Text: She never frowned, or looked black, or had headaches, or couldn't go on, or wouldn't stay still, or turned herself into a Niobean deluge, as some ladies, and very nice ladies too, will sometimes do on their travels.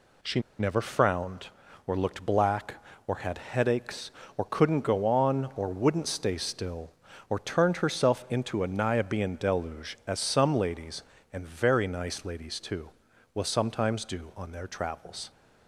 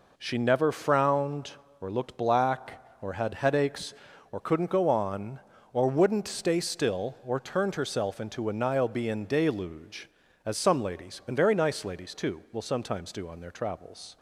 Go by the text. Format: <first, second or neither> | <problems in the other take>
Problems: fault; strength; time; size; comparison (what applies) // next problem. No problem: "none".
second | pauses between "She" and "never"; slight; at 0.3 s; 0.20 s long